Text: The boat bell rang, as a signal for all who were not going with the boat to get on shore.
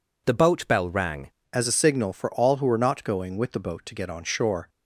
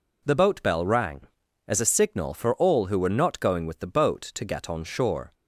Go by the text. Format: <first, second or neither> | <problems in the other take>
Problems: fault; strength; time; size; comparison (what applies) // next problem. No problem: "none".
second | changes voice at "as"; from 1.5 s on; 3.1 s long